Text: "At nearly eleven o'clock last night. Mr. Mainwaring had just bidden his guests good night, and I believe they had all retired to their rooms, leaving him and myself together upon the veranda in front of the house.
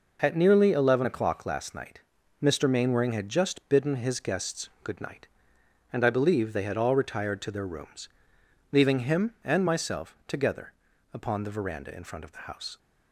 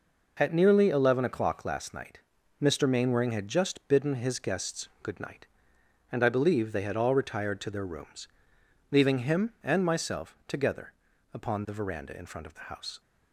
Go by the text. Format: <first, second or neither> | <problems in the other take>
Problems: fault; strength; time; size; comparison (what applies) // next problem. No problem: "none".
neither | pauses between "together" and "upon"; the same in both